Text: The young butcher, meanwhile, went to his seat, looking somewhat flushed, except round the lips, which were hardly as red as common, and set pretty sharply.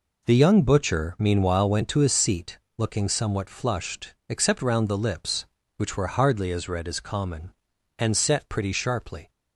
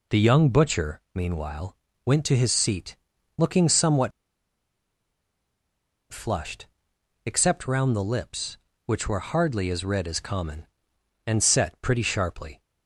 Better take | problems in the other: first | pauses between "somewhat" and "flushed"; strong; at 4.1 s; 2.0 s long

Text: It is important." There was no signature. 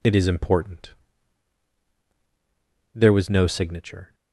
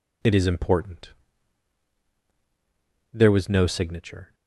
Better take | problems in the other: neither | none

